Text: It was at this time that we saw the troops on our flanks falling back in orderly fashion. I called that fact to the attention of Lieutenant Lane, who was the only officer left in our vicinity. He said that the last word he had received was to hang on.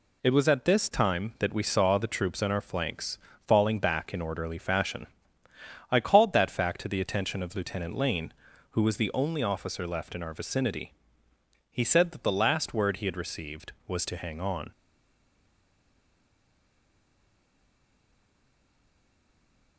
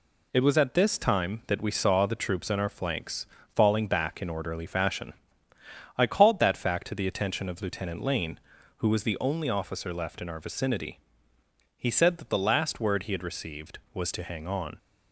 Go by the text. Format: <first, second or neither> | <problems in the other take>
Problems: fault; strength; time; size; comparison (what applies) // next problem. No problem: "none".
second | pauses between "flanks" and "falling"; slight; at 3.1 s; 0.30 s long; slight in the second // stays silent after the last word; strong; from 14.7 s on; 5.0 s long